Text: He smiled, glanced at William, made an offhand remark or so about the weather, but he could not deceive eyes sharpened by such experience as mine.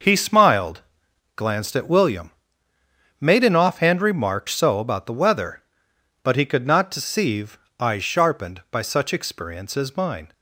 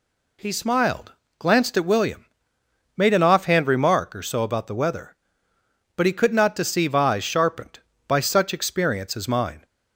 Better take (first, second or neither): second